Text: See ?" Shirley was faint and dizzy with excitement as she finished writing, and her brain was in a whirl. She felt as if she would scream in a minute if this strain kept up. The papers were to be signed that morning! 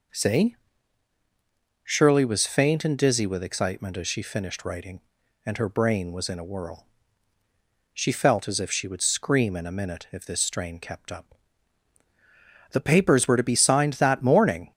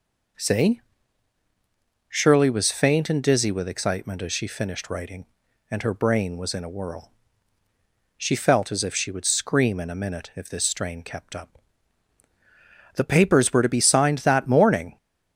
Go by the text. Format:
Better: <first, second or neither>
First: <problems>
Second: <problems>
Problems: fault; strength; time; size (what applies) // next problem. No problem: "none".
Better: neither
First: none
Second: none